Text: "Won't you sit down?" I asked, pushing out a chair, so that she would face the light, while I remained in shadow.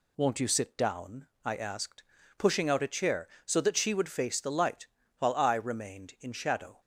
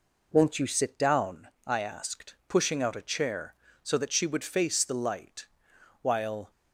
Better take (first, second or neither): first